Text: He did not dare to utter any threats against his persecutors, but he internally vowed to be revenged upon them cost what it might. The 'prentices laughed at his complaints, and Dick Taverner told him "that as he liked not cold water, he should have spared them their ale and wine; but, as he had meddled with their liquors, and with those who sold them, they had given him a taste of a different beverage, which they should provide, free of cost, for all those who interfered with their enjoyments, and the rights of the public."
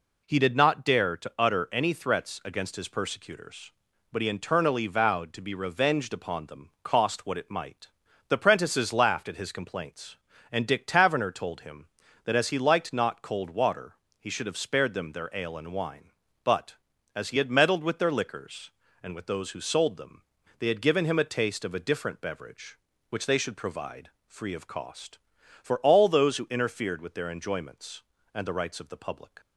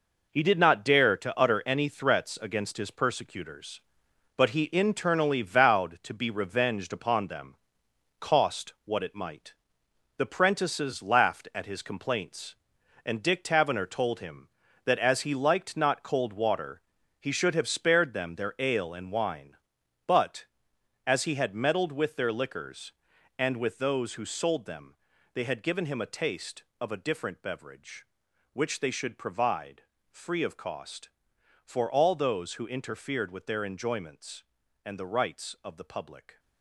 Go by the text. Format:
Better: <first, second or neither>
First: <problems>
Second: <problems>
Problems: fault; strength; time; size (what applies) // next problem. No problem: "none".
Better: first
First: none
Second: gets quieter; strong; throughout; 8.5 dB // pauses between "them" and "cost"; noticeable; at 7.5 s; 0.66 s long